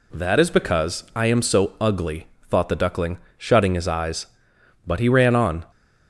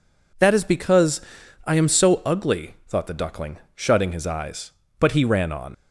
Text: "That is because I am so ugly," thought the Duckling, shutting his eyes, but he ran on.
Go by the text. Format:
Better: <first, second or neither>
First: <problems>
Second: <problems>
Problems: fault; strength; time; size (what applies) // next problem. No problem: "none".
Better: first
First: none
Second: pauses between "because" and "I"; at 1.1 s; 0.44 s long // leaves "on" unfinished; at 5.7 s; 55 ms